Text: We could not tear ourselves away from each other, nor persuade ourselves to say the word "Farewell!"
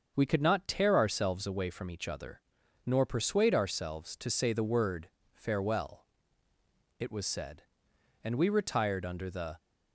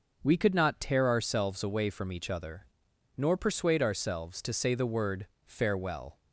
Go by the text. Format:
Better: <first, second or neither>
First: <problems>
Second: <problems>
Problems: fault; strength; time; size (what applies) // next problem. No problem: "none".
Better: second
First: starts louder than the rest; until 1.1 s; 6.5 dB // pauses between "word" and "Farewell"; slight; at 5.0 s; 0.24 s long // goes on to say "It was said and we retired under the"; strong; from 6.9 s on; 2.5 s long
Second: pauses between "word" and "Farewell"; slight; at 5.2 s; 0.20 s long